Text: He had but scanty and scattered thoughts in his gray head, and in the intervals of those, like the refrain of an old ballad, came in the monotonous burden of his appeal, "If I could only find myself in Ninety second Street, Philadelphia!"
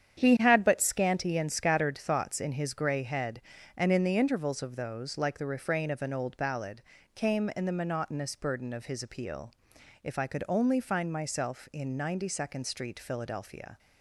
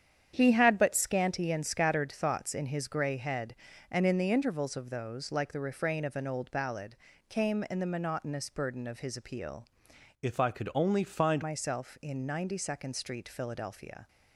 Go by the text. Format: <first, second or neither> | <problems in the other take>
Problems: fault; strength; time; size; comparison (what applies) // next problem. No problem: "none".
first | starts louder than the rest; strong; until 1.3 s; 9 dB; strong in the first // changes voice from "If" to "find"; from 10.2 to 11.4 s; 1.2 s long